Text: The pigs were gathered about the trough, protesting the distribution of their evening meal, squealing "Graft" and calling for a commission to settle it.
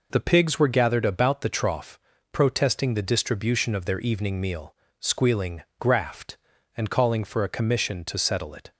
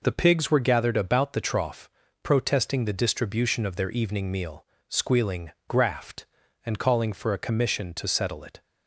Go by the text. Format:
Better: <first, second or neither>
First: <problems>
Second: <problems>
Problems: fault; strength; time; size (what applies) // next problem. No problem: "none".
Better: neither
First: pauses between "squealing" and "Graft"; slight; at 5.6 s; 0.16 s long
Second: pauses between "squealing" and "Graft"; slight; at 5.5 s; 0.16 s long